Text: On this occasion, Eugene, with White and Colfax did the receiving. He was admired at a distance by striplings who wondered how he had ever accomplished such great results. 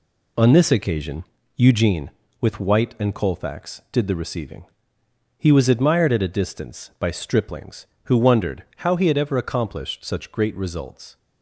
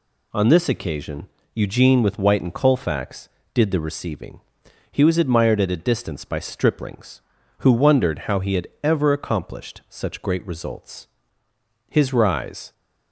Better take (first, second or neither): first